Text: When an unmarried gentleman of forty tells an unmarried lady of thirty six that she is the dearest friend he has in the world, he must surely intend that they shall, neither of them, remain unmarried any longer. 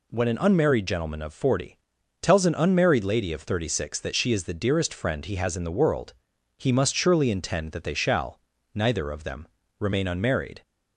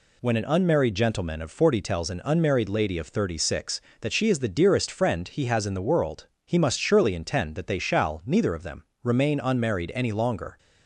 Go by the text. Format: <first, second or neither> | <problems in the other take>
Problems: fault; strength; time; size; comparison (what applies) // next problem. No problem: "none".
second | pauses between "forty" and "tells"; at 1.7 s; 0.42 s long // stops before "any longer"; at 10.6 s